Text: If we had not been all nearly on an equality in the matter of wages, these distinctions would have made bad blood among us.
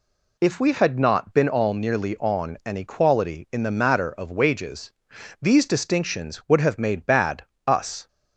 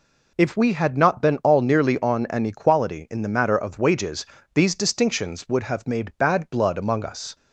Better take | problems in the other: second | skips "blood among"; at 7.5 s

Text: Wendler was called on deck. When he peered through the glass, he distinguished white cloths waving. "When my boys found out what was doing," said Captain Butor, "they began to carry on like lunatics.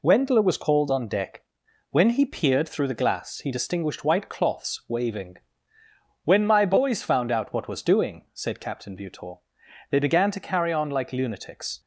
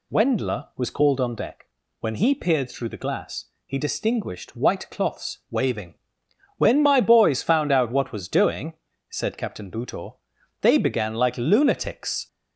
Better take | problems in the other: first | skips "to carry on"; at 11.1 s

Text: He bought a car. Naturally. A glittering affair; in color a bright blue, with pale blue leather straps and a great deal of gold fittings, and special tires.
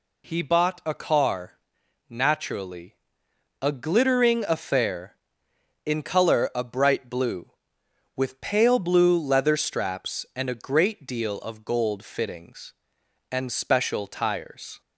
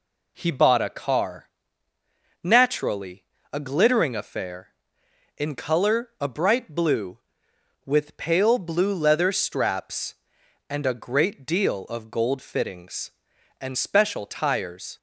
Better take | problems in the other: neither | none

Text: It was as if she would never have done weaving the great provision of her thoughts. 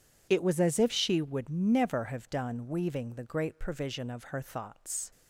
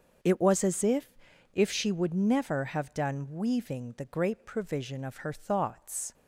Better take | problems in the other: first | starts louder than the rest; until 1.7 s; 7 dB // says "if" twice; at 1.5 s

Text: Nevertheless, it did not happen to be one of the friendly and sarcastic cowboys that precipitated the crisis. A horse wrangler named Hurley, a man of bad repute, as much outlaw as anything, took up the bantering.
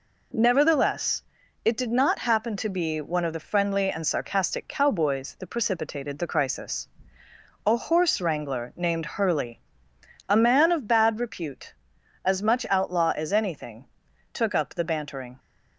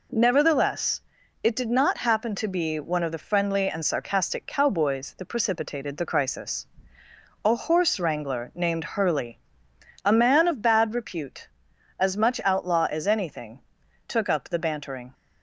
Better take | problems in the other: neither | none

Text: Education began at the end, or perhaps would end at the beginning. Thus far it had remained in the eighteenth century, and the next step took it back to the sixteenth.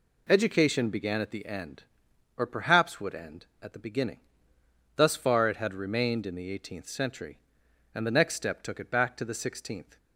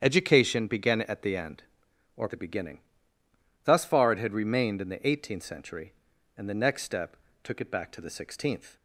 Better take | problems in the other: first | starts louder than the rest; strong; until 1.0 s; 8.5 dB // skips "perhaps would end at"; at 2.2 s // pauses between "step" and "took"; slight; at 7.1 s; 0.28 s long

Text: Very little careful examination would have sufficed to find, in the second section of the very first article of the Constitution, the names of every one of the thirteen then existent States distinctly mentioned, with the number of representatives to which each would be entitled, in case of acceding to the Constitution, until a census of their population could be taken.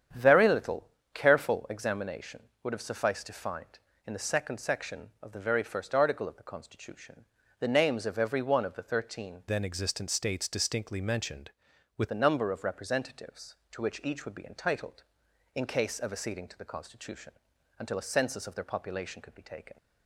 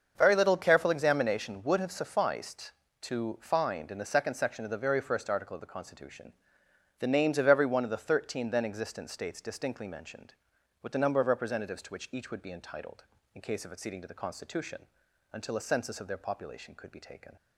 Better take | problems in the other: second | starts louder than the rest; strong; until 1.4 s; 8.5 dB; also in the second // pauses between "little" and "careful"; slight; at 0.8 s; 0.24 s long // changes voice from "then" to "with"; from 9.4 to 12.1 s; 2.7 s long

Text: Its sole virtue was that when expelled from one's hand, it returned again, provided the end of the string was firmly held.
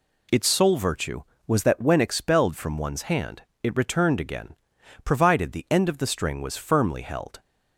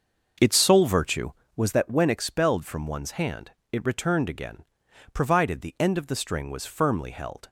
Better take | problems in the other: first | starts louder than the rest; noticeable; until 1.5 s; 6 dB

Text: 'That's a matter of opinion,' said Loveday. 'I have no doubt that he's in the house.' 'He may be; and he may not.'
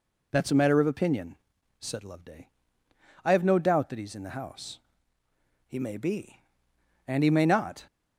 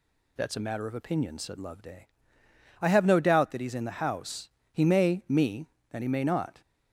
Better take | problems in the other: first | says "me" for "be"; at 5.2 s

